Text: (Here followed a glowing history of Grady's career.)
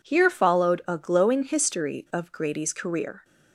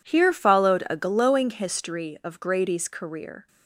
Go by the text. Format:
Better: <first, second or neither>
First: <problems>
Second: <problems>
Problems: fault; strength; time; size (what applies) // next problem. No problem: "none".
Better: neither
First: none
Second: none